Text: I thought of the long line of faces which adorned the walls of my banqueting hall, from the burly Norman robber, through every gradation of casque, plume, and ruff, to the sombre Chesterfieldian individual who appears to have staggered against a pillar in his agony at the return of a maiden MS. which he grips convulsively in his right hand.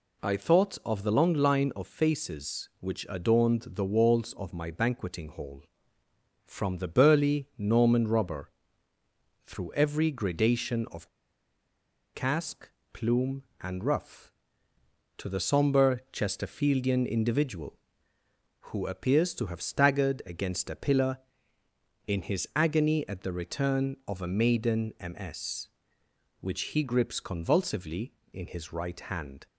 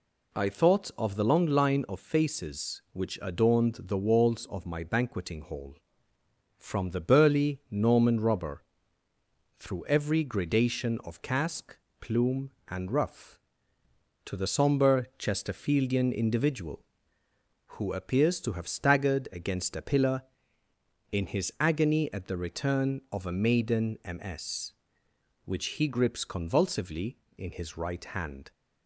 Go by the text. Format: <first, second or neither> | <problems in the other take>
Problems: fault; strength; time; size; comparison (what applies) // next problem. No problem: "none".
second | pauses between "of" and "casque"; at 11.0 s; 1.0 s long